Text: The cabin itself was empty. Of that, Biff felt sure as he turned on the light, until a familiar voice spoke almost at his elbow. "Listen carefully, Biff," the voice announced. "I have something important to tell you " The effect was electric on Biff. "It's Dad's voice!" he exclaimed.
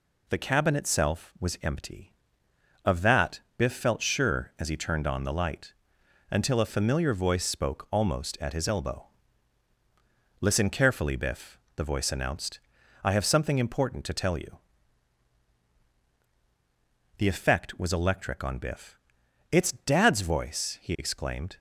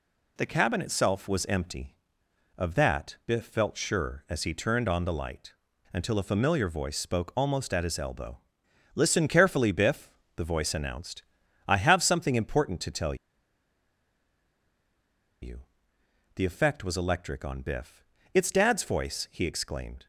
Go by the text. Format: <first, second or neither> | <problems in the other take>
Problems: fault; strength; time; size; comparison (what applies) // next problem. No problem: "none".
first | pauses between "tell" and "you"; strong; at 13.1 s; 2.2 s long